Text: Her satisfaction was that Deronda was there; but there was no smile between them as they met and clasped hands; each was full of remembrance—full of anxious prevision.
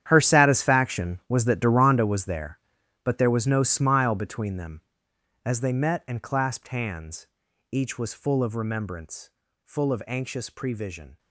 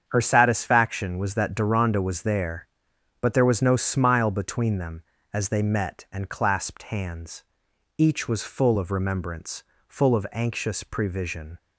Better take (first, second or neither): second